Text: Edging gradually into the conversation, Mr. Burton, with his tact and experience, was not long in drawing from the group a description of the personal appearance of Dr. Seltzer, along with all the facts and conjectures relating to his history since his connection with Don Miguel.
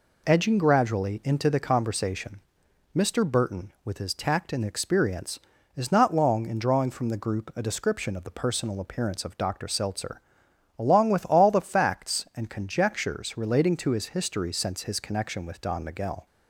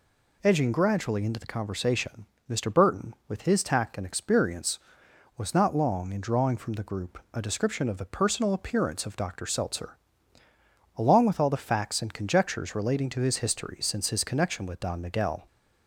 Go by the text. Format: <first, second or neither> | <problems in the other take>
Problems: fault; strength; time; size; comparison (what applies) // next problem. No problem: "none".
second | says "is" for "was"; at 5.7 s